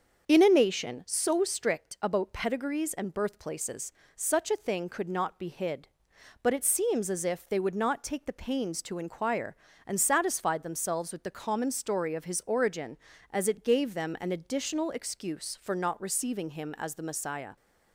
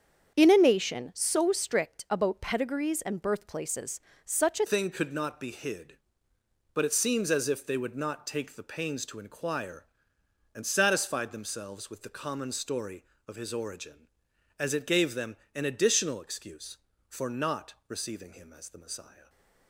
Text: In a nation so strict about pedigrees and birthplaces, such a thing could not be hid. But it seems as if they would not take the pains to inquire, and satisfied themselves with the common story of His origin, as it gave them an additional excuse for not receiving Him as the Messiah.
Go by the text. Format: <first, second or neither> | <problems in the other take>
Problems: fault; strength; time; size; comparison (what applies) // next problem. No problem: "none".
first | starts louder than the rest; strong; until 1.3 s; 7.5 dB; also in the first // changes voice at "thing"; from 4.6 s on; 14.6 s long // pauses between "them" and "an"; slight; at 15.3 s; 0.18 s long